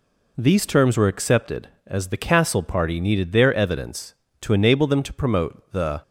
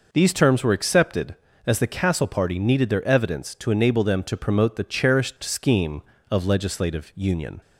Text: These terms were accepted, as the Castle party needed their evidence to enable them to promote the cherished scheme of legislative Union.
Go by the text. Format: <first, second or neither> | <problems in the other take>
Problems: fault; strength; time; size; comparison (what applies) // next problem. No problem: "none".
second | stops before "cherished scheme of legislative Union"; at 6.0 s